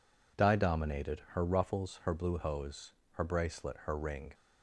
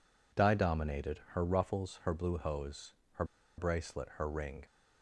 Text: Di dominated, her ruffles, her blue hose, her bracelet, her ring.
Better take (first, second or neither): first